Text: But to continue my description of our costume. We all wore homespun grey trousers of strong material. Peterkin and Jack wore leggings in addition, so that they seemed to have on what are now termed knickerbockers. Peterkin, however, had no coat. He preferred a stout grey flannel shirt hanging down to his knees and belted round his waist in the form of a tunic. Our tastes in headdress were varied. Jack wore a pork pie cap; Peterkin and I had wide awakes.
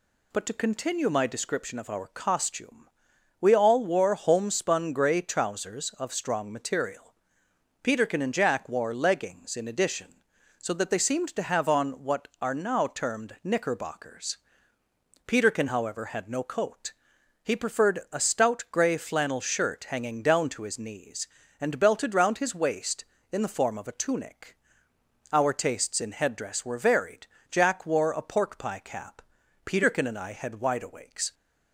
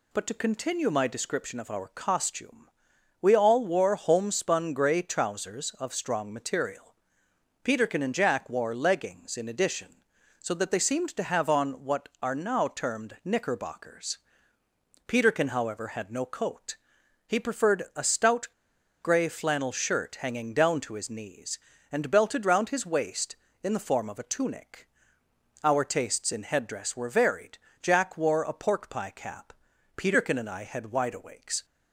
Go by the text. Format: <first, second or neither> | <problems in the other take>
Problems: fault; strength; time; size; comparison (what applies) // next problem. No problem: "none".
first | pauses between "stout" and "grey"; noticeable; at 18.4 s; 0.55 s long